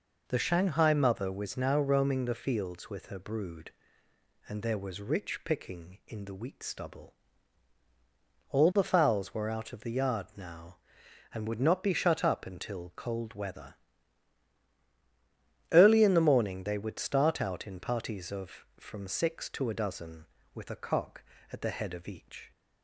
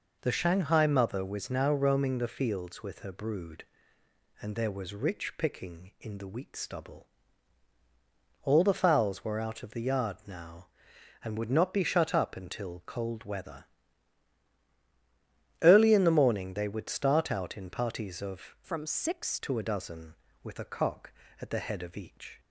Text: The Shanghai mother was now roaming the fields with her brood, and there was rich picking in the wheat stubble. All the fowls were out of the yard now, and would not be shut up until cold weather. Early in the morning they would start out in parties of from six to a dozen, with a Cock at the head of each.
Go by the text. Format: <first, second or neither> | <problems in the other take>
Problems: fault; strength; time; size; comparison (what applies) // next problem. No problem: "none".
first | changes voice from "from" to "six"; from 18.6 to 19.3 s; 0.7 s long